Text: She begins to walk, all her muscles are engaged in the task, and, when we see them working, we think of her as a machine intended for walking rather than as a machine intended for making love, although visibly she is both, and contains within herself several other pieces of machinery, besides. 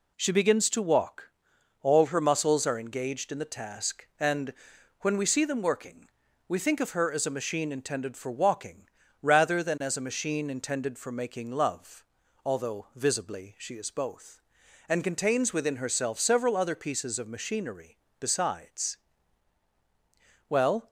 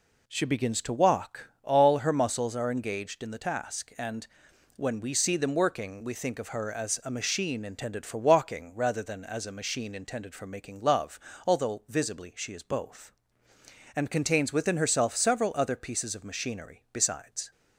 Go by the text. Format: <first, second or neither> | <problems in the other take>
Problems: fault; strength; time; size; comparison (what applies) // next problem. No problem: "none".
second | pauses between "walking" and "rather"; slight; at 8.8 s; 0.36 s long // goes on to say "Well"; slight; from 20.4 s on; 0.42 s long